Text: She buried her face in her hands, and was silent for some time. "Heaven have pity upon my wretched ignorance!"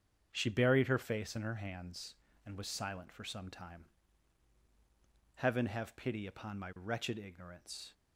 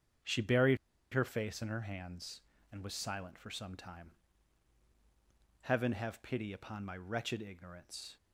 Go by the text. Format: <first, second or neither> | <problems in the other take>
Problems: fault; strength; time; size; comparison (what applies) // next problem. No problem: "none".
first | starts louder than the rest; strong; until 1.6 s; 7.5 dB; strong in the first // pauses between "buried" and "her"; at 0.7 s; 0.37 s long